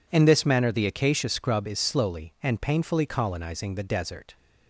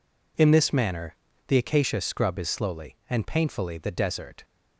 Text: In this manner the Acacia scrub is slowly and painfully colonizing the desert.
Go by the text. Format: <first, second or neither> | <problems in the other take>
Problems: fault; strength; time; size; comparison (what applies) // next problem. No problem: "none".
first | pauses between "manner" and "the"; slight; at 1.1 s; 0.32 s long // skips "colonizing"; at 3.7 s